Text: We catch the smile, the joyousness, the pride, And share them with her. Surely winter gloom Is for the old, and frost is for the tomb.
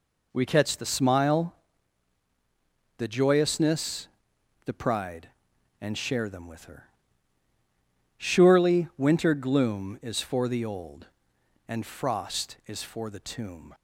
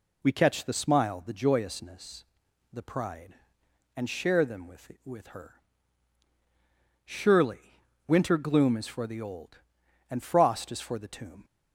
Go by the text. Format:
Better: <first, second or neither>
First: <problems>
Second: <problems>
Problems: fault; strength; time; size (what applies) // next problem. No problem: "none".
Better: first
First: none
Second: says "with" twice; at 5.0 s // pauses between "Surely" and "winter"; slight; at 7.8 s; 0.26 s long